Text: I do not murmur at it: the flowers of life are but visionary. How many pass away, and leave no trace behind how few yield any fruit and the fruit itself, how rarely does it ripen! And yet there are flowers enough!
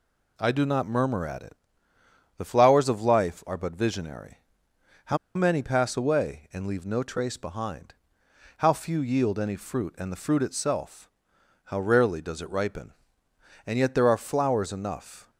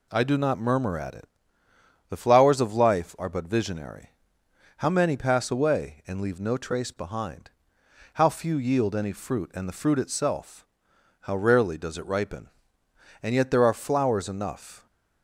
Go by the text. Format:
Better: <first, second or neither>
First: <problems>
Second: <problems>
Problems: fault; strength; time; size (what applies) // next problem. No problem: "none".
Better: second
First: pauses between "How" and "many"; slight; at 5.1 s; 0.19 s long // pauses between "behind" and "how"; noticeable; at 7.9 s; 0.64 s long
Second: pauses between "behind" and "how"; noticeable; at 7.5 s; 0.64 s long